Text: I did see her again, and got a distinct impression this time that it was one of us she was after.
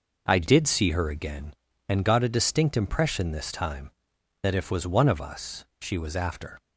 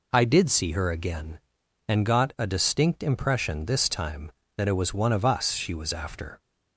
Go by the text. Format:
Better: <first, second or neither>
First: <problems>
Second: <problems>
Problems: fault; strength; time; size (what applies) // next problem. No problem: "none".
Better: second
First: says "if" for "it"; at 4.5 s // pauses between "us" and "she"; slight; at 5.6 s; 0.16 s long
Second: none